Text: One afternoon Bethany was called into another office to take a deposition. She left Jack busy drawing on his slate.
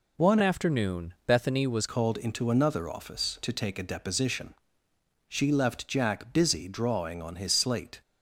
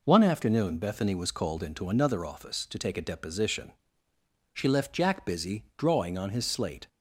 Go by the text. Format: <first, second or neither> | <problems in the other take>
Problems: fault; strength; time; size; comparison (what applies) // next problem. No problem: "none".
second | changes voice from "afternoon" to "was"; from 0.4 to 1.8 s; 1.4 s long